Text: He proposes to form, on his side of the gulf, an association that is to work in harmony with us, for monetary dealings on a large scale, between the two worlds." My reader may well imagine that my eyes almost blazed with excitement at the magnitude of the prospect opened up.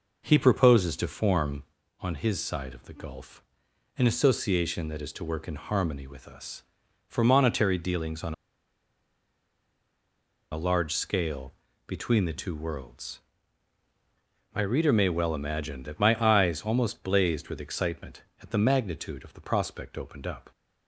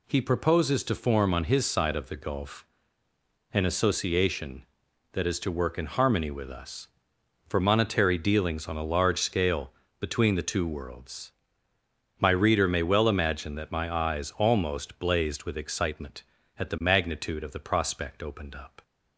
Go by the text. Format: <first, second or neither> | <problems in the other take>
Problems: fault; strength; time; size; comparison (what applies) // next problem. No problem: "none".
second | pauses between "on" and "a"; strong; at 8.3 s; 2.1 s long